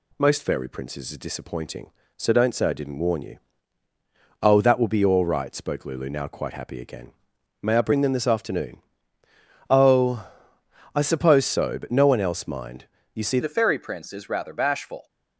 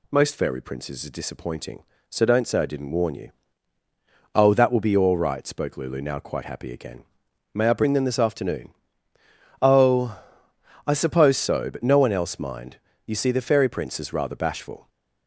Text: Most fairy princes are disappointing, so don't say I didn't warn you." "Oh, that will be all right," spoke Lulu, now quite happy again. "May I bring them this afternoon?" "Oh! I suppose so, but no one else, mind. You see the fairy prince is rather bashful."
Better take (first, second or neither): second